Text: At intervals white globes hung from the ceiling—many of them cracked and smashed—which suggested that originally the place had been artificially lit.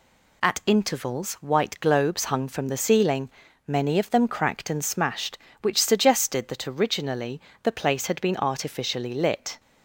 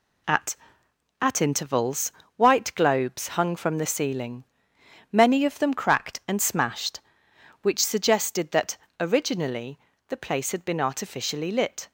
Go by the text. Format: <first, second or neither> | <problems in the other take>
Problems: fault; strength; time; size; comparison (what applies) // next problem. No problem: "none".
first | says "At" twice; at 1.2 s // pauses between "intervals" and "white"; slight; at 2.1 s; 0.26 s long // pauses between "that" and "originally"; slight; at 8.7 s; 0.20 s long // pauses between "originally" and "the"; slight; at 9.7 s; 0.30 s long; slight in the first